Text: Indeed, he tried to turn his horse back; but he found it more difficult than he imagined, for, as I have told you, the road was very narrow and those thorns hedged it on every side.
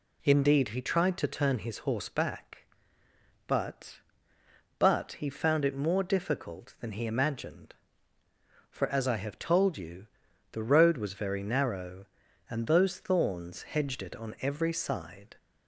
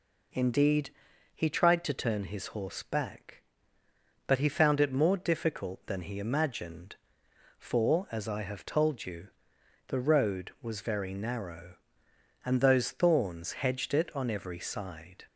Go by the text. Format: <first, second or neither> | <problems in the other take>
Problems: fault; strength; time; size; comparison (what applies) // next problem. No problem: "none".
second | says "but" twice; at 4.7 s